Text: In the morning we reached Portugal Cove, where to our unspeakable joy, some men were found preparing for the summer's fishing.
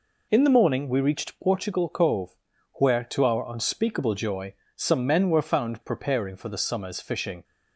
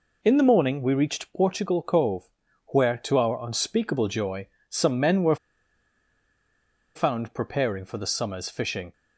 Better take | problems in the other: first | pauses between "were" and "found"; strong; at 5.3 s; 1.6 s long

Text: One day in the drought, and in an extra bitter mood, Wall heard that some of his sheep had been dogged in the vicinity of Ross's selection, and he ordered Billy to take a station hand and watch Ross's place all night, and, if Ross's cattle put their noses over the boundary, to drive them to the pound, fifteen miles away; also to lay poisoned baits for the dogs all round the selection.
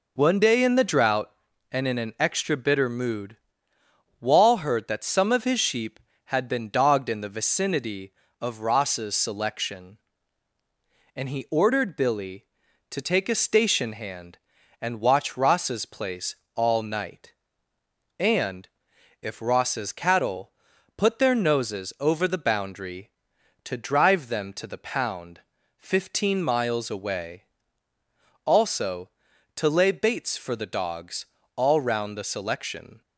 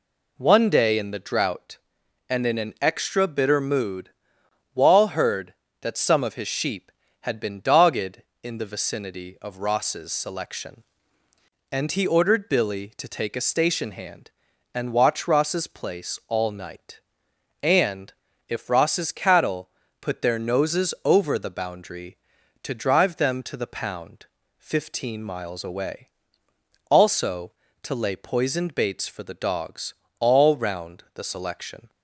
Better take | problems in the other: second | pauses between "place" and "all"; slight; at 16.3 s; 0.20 s long // pauses between "cattle" and "put"; noticeable; at 20.4 s; 0.48 s long; slight in the second // skips "poisoned"; at 29.9 s // pauses between "dogs" and "all"; slight; at 31.2 s; 0.30 s long; slight in the second

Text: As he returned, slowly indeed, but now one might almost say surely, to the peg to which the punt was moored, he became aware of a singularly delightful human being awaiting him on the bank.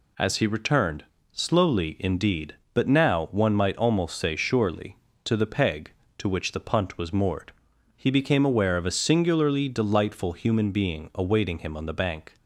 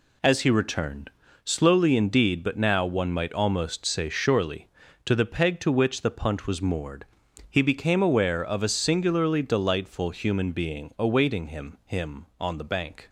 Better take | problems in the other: first | says "him" twice; at 11.8 s

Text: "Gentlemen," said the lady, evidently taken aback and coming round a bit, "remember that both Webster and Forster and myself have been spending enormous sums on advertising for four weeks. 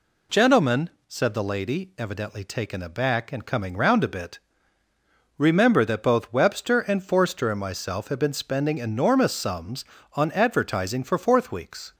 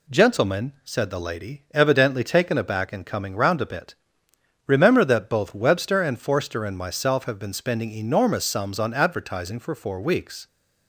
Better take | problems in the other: second | says "fourth" for "four"; at 11.1 s

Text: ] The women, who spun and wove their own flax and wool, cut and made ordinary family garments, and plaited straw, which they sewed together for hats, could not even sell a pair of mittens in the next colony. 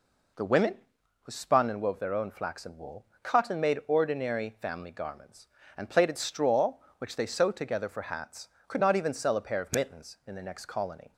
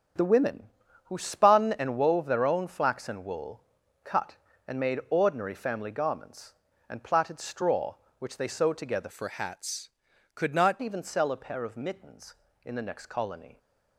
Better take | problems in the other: first | starts louder than the rest; strong; until 1.5 s; 7.5 dB // changes voice from "for" to "not"; from 9.1 to 10.7 s; 1.6 s long

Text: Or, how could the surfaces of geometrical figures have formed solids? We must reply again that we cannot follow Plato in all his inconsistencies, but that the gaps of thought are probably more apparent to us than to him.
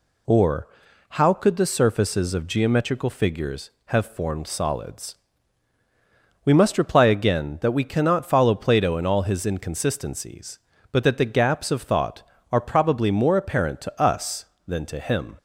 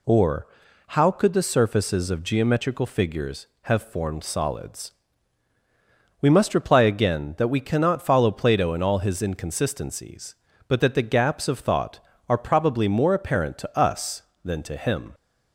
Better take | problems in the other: neither | none

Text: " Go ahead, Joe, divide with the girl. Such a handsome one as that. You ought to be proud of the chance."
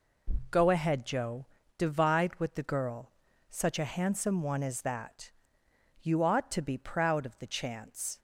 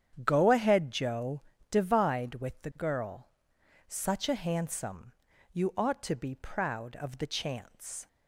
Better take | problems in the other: first | starts louder than the rest; strong; until 1.1 s; 9 dB // skips "one as that"; at 5.3 s

